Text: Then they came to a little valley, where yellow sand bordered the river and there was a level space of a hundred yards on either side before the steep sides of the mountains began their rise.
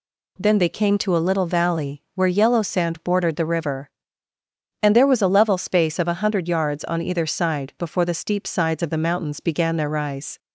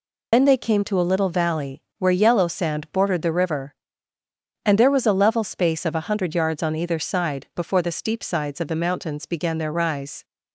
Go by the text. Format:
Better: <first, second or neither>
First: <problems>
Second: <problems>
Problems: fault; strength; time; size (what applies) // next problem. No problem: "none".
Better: first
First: none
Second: loses the start of "Then"; at 0.3 s; 90 ms